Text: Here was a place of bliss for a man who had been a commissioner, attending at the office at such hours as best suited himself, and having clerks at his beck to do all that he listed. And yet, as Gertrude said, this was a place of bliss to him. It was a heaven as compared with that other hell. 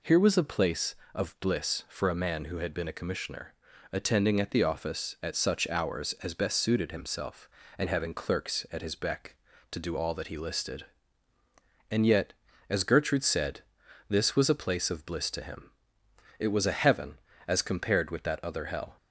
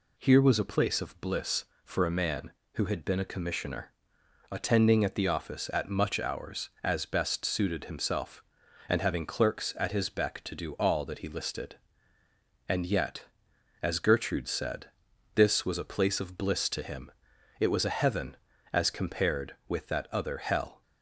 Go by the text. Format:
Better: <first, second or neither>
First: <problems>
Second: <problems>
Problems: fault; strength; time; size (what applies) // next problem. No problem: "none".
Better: first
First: none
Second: says "much" for "such"; at 5.8 s